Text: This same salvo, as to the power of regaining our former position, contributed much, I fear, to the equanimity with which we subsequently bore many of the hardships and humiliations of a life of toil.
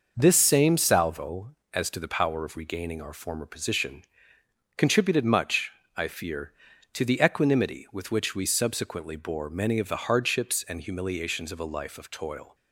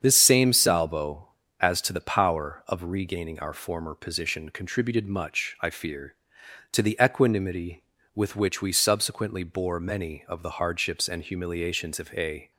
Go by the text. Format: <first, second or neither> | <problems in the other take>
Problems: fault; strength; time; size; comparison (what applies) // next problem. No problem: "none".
first | starts louder than the rest; strong; until 1.0 s; 8 dB // stops before "life of toil"; at 12.5 s